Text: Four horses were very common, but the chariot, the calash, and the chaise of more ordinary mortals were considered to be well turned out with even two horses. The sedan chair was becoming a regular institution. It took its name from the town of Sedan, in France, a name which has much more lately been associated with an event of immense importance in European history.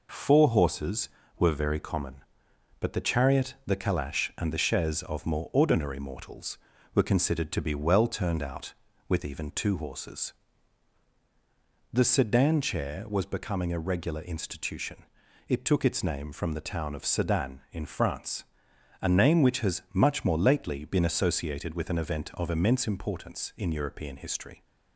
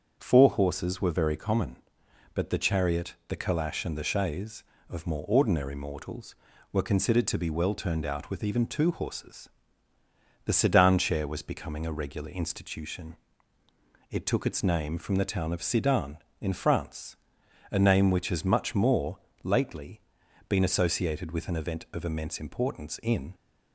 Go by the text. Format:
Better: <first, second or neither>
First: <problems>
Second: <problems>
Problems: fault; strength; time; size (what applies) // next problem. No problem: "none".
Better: first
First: none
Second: starts louder than the rest; until 1.1 s; 7 dB // pauses between "more" and "lately"; slight; at 19.1 s; 0.24 s long // pauses between "lately" and "been"; noticeable; at 20.0 s; 0.46 s long // stops before "European history"; at 23.3 s